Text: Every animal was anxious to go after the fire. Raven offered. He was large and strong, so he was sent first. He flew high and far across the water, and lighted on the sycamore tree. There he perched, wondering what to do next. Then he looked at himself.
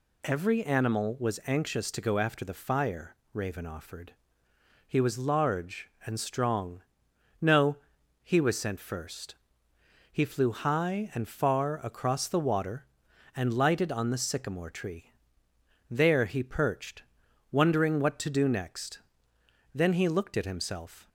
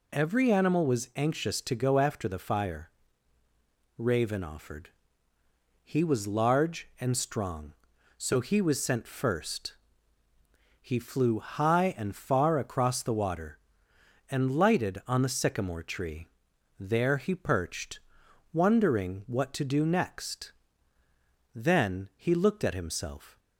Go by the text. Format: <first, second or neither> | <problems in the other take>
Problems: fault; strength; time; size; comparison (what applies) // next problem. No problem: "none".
second | says "no" for "so"; at 7.3 s